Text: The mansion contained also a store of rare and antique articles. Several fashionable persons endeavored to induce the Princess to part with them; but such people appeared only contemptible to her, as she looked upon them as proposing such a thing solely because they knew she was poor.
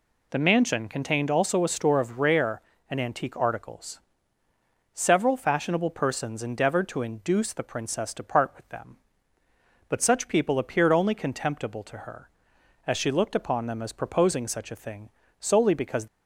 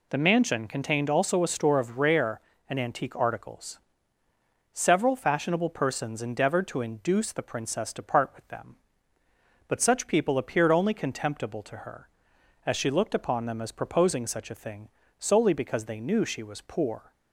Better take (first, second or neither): second